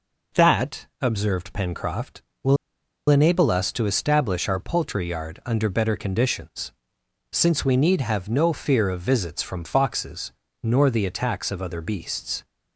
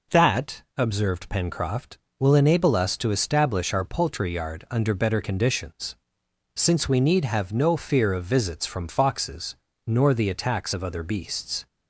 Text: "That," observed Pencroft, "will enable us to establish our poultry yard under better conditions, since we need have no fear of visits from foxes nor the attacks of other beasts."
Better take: second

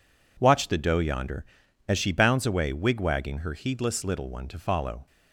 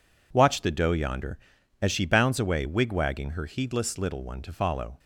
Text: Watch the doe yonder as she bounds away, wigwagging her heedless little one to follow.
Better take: neither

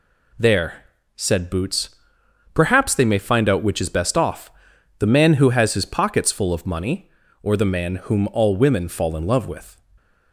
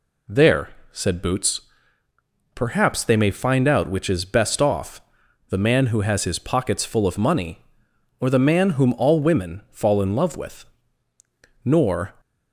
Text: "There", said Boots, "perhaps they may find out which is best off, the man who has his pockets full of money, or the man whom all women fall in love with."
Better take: first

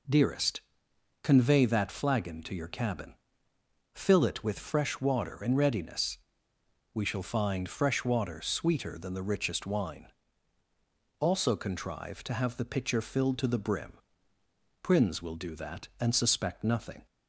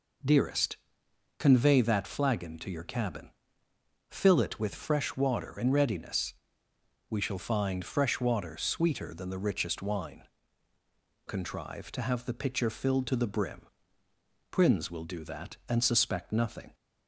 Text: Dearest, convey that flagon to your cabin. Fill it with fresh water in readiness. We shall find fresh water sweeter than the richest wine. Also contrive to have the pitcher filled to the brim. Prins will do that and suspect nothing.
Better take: first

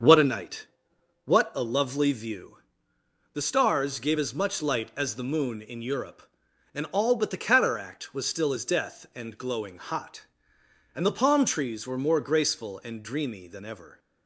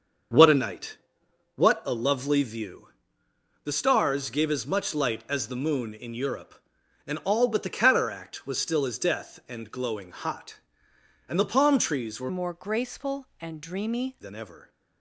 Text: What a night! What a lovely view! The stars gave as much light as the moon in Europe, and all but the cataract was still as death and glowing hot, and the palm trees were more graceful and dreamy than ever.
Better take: first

